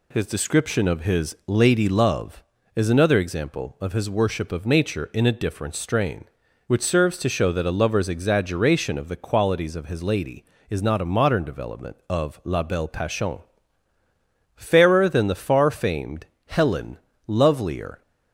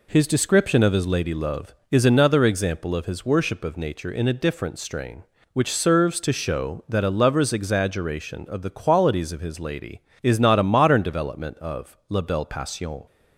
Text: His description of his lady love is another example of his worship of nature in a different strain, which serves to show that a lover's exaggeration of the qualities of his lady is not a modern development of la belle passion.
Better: second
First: goes on to say "Fairer than the far famed Helen Lovelier"; strong; from 14.5 s on; 3.4 s long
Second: none

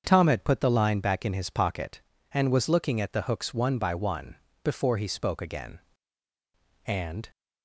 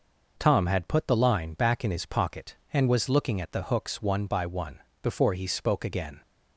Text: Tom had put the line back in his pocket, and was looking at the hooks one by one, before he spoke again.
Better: second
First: starts louder than the rest; until 1.0 s; 7 dB // goes on to say "And"; slight; from 6.8 s on; 0.44 s long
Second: none

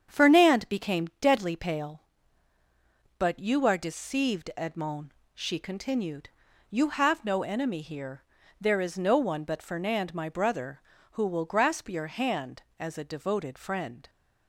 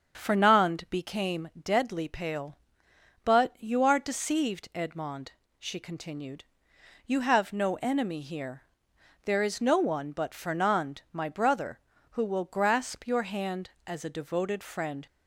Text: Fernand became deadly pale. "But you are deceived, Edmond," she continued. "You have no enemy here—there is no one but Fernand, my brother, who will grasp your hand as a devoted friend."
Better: neither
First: starts louder than the rest; strong; until 1.2 s; 7.5 dB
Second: starts louder than the rest; until 1.1 s; 7 dB

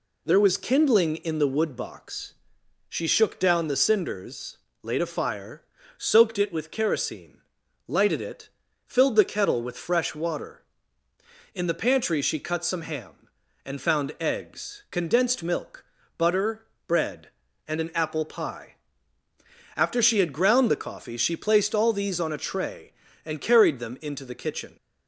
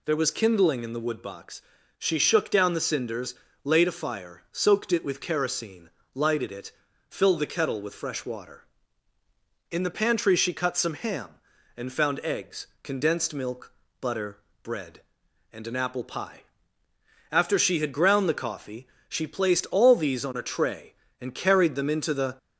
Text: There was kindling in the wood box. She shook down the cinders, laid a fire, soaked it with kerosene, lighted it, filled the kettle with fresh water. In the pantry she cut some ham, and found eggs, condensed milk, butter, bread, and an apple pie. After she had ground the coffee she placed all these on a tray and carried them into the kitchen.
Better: first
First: none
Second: pauses between "coffee" and "she"; slight; at 18.8 s; 0.22 s long // stops before "kitchen"; at 22.3 s

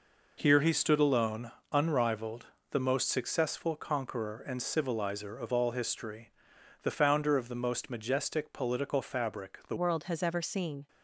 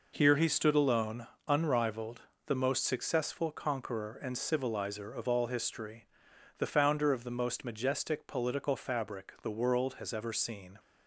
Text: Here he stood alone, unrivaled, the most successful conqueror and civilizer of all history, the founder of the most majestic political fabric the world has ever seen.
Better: second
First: changes voice at "world"; from 9.7 s on; 1.1 s long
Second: none

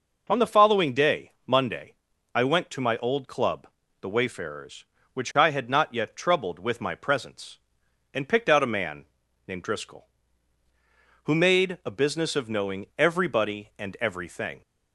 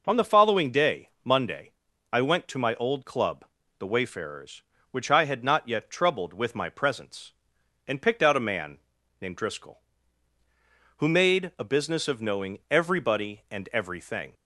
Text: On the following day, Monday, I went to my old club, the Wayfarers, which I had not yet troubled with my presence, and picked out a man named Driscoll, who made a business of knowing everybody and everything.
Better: neither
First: pauses between "man" and "named"; at 9.0 s; 0.42 s long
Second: pauses between "man" and "named"; at 8.7 s; 0.42 s long

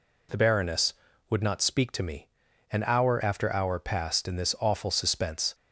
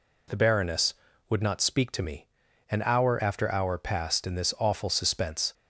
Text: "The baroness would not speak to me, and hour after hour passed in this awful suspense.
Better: neither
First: none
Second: none

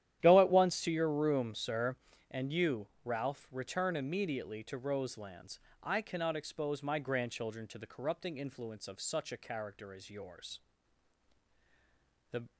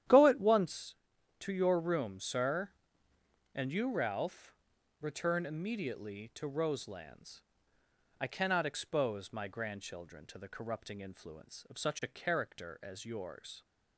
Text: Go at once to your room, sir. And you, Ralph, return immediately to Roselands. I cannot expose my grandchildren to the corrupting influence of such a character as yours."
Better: second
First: starts louder than the rest; strong; until 1.2 s; 11.5 dB // goes on to say "The"; slight; from 12.2 s on; 0.22 s long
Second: starts louder than the rest; strong; until 1.5 s; 11 dB

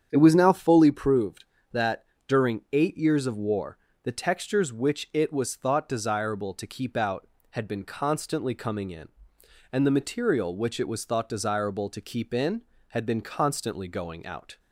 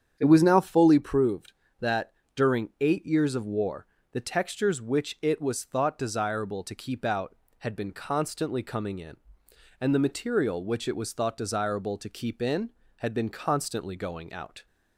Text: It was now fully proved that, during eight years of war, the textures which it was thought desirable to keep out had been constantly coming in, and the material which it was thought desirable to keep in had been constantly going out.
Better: neither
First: starts louder than the rest; strong; until 1.1 s; 8 dB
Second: starts louder than the rest; strong; until 1.1 s; 8 dB

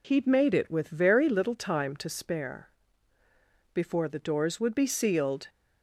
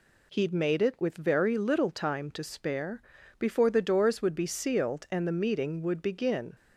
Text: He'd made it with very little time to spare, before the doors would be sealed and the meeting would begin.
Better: second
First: stops before "and the meeting would begin"; at 5.4 s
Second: none

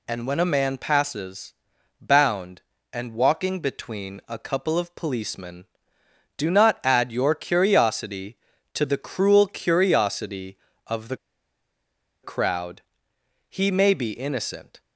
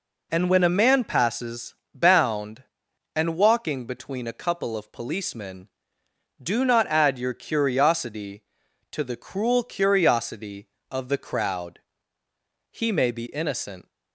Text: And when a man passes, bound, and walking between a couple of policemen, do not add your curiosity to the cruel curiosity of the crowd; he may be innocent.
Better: second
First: pauses between "the" and "crowd"; at 11.1 s; 1.0 s long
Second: none

